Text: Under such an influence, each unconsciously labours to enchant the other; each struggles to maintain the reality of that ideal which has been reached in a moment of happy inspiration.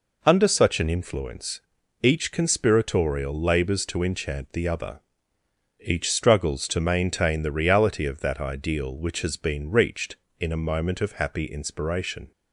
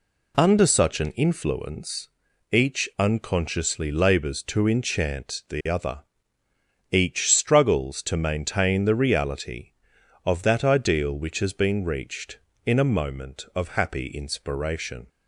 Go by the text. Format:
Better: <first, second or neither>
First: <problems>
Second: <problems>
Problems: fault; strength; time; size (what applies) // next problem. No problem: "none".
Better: second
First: says "conspiratorial" for "unconsciously"; at 2.3 s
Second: none